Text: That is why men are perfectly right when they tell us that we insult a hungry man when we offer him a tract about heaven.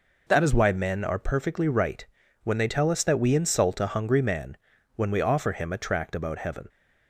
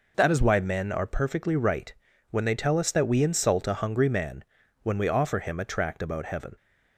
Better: neither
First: pauses between "right" and "when"; at 2.0 s; 0.38 s long // pauses between "man" and "when"; at 4.5 s; 0.38 s long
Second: pauses between "right" and "when"; at 1.9 s; 0.37 s long // pauses between "man" and "when"; at 4.4 s; 0.38 s long

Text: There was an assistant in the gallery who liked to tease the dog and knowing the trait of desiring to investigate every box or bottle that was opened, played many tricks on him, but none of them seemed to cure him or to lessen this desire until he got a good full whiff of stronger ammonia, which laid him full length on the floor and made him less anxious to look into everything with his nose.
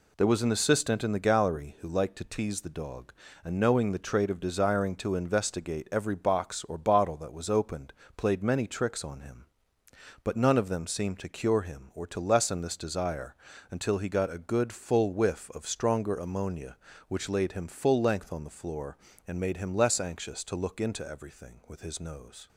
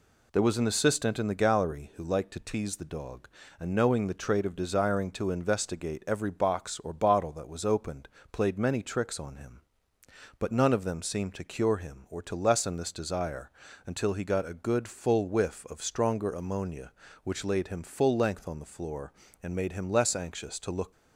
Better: first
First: pauses between "desire" and "until"; at 13.3 s; 0.38 s long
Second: pauses between "desire" and "until"; at 13.4 s; 0.38 s long // stops before "into everything with his nose"; at 20.9 s

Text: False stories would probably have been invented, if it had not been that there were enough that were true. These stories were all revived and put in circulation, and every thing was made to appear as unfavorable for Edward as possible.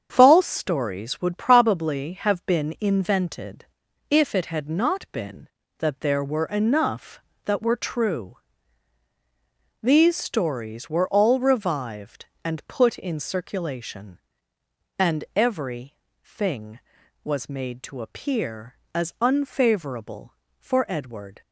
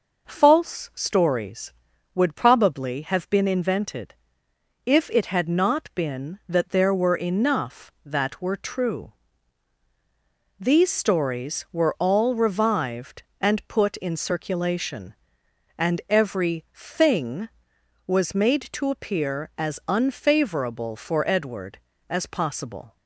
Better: second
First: starts louder than the rest; strong; until 1.1 s; 7.5 dB // pauses between "every" and "thing"; slight; at 15.9 s; 0.32 s long // stops before "as possible"; at 21.4 s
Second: none

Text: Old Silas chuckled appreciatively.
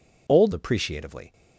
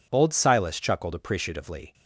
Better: second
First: skips "Silas chuckled"; at 0.5 s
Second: none

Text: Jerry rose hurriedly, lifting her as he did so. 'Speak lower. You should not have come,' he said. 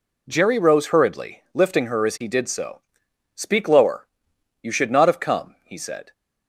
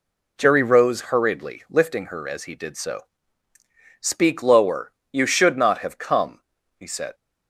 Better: neither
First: none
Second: none

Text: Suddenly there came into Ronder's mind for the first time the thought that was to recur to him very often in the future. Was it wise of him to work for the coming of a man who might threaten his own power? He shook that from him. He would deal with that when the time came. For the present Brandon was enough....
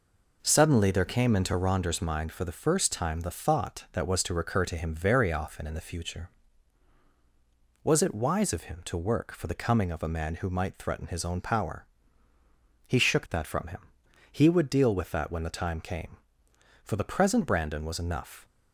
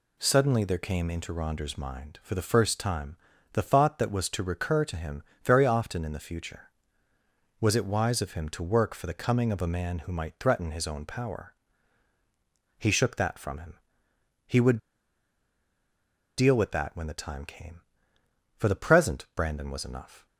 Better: first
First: none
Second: pauses between "time" and "the"; slight; at 3.1 s; 0.36 s long // pauses between "him" and "very"; slight; at 5.2 s; 0.22 s long // pauses between "would" and "deal"; strong; at 14.7 s; 1.6 s long

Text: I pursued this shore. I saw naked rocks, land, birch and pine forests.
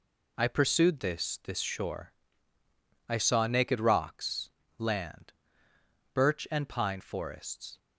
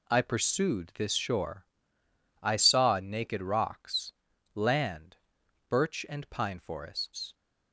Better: second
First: says "this" twice; at 1.4 s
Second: none

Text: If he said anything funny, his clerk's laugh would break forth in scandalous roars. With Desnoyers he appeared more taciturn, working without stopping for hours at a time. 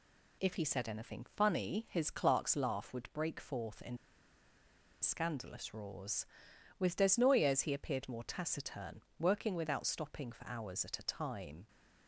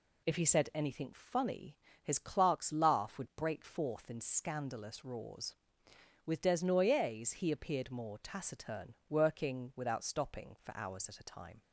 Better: second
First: pauses between "in" and "scandalous"; at 3.9 s; 1.0 s long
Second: none

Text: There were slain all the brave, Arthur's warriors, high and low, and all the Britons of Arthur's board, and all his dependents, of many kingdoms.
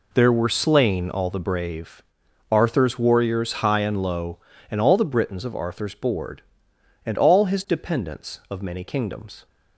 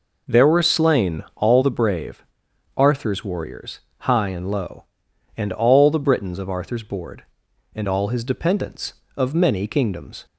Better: neither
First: none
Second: none

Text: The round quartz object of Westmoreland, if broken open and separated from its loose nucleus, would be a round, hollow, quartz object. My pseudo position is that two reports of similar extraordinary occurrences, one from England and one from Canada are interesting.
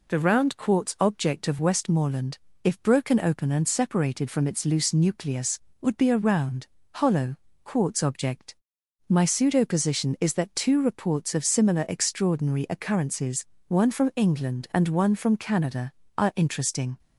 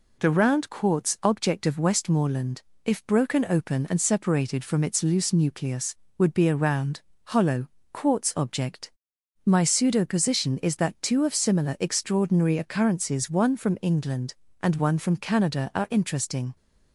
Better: first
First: none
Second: skips "reports"; at 11.2 s

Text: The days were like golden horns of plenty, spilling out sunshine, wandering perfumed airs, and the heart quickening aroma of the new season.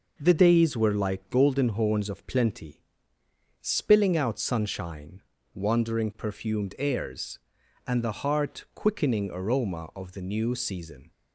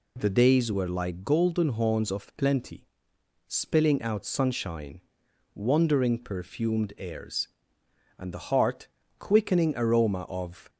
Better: first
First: none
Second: pauses between "heart" and "quickening"; slight; at 8.8 s; 0.32 s long // stops before "the new season"; at 10.6 s

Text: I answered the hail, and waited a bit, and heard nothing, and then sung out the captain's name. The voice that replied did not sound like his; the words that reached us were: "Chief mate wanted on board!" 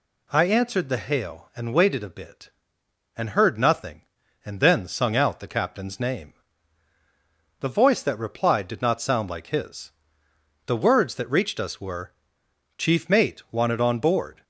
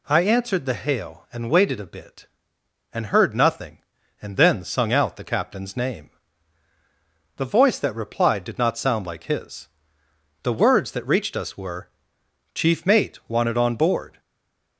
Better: first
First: none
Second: stays silent after the last word; slight; from 14.1 s on; 0.6 s long

